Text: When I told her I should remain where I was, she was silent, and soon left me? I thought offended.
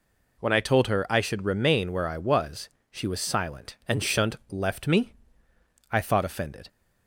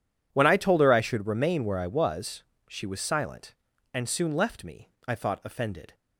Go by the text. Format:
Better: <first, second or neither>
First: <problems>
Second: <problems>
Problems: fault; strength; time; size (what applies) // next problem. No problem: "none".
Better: second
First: says "shunt" for "soon"; at 4.0 s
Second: none